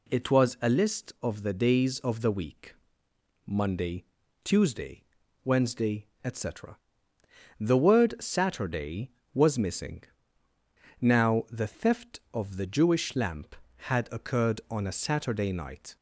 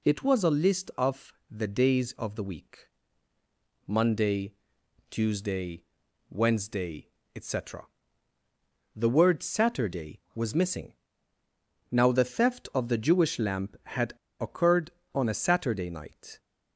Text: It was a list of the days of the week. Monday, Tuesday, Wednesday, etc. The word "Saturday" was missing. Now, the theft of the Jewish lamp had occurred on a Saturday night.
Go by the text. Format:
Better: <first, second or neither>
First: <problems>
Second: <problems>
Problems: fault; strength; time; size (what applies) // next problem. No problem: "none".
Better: first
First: none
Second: pauses between "of" and "the"; slight; at 1.3 s; 0.18 s long // pauses between "had" and "occurred"; slight; at 14.1 s; 0.29 s long